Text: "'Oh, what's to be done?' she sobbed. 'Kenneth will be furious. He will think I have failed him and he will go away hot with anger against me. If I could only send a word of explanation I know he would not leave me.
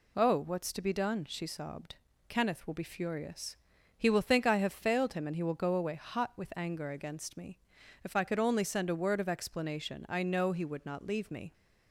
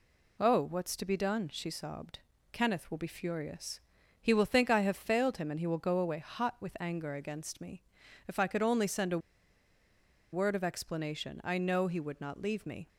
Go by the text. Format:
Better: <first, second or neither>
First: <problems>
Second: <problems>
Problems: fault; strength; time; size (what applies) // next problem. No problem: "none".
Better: first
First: none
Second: pauses between "a" and "word"; at 9.1 s; 1.1 s long